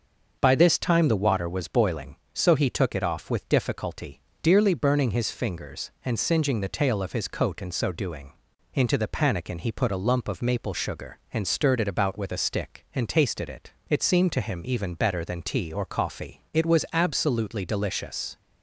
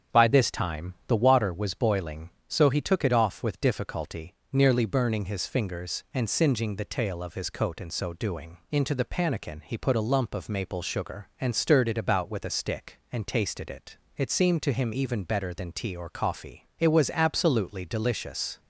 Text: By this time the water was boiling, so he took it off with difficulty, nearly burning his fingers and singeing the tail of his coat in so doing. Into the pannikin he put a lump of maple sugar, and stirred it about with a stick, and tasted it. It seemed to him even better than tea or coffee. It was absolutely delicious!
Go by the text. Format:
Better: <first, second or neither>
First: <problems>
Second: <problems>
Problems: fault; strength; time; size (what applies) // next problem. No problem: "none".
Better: second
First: starts louder than the rest; until 1.4 s; 6 dB // says "dearly" for "nearly"; at 4.4 s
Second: starts louder than the rest; strong; until 1.2 s; 7.5 dB